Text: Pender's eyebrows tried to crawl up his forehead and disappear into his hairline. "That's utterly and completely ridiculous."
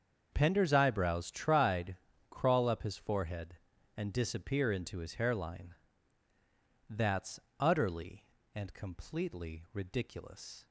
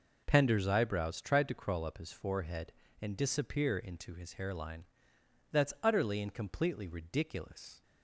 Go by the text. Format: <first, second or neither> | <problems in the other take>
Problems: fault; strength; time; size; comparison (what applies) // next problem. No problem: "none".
second | starts louder than the rest; until 1.3 s; 7 dB // skips "to"; at 2.1 s // pauses between "That's" and "utterly"; slight; at 7.3 s; 0.19 s long